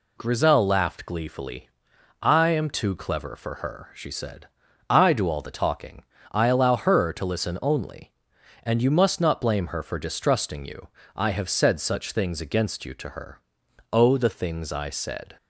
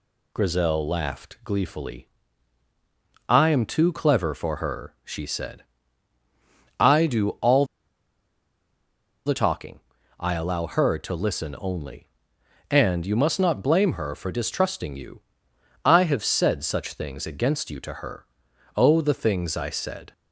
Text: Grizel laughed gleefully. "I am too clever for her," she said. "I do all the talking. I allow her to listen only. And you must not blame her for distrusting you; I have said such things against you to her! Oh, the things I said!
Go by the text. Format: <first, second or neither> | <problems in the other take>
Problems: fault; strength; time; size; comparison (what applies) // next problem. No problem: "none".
first | pauses between "all" and "the"; strong; at 7.6 s; 1.5 s long